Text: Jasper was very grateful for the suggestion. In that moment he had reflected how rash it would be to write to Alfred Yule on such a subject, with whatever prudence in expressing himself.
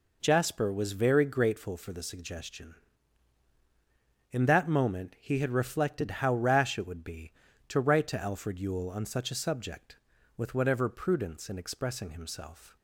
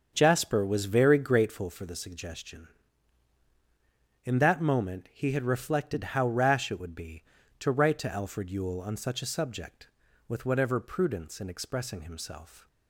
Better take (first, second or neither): first